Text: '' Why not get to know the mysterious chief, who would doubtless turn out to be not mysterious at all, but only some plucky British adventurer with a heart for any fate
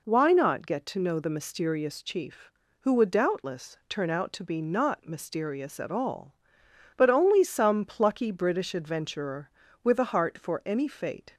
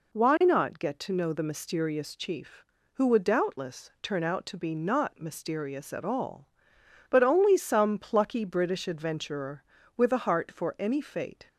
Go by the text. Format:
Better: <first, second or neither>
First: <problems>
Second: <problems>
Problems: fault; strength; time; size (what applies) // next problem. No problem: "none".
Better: neither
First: none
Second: none